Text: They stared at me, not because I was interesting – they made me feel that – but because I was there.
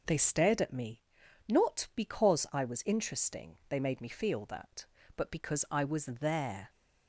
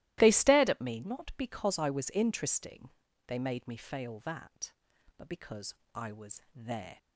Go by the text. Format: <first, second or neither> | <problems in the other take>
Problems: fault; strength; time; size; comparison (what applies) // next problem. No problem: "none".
first | starts louder than the rest; strong; until 1.2 s; 16 dB // says "fail" for "feel"; at 3.7 s // pauses between "because" and "I"; slight; at 5.7 s; 0.18 s long